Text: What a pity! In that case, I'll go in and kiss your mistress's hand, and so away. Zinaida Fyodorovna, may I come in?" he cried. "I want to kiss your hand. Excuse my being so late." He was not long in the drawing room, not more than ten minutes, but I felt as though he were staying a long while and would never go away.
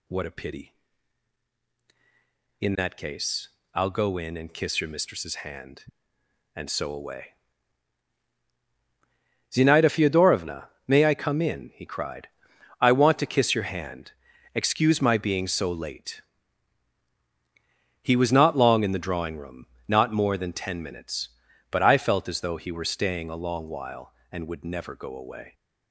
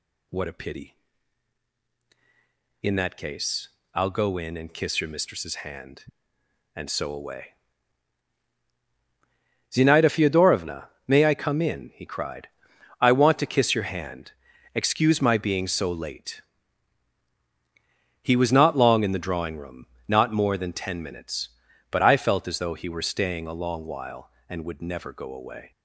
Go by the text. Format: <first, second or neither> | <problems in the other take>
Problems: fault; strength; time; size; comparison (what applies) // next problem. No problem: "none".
neither | none